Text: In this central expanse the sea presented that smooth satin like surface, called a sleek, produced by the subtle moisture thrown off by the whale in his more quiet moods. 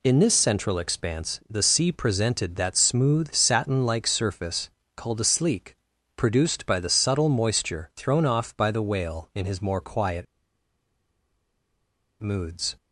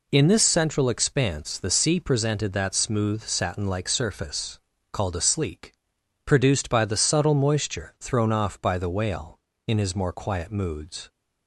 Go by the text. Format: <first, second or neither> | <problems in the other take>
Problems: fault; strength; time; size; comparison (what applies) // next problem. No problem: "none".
second | pauses between "quiet" and "moods"; strong; at 10.2 s; 1.9 s long